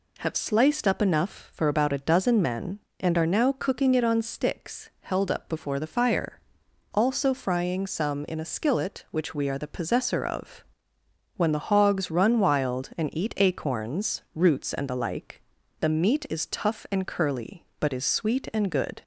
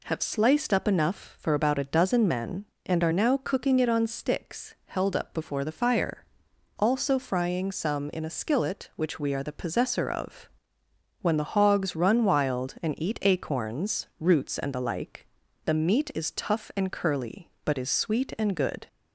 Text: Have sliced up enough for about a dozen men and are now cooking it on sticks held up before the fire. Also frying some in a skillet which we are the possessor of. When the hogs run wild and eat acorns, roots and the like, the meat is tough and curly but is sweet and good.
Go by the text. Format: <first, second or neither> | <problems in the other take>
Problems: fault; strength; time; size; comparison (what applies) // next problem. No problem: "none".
neither | none